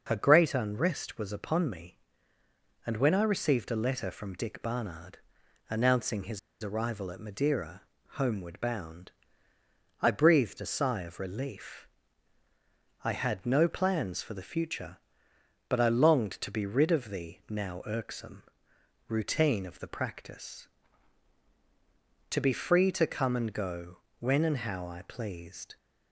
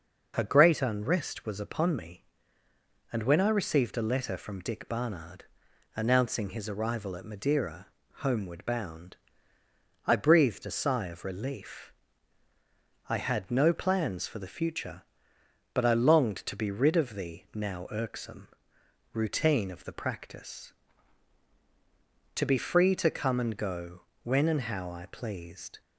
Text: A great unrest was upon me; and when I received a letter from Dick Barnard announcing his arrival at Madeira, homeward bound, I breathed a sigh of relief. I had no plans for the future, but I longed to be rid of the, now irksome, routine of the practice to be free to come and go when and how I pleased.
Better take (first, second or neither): second